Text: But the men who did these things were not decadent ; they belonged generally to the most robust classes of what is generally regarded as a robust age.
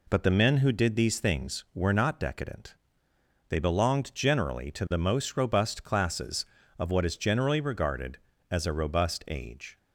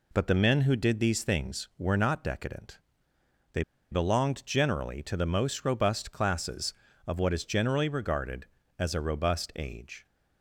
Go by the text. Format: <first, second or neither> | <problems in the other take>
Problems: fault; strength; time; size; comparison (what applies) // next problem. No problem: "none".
first | pauses between "they" and "belonged"; slight; at 3.6 s; 0.29 s long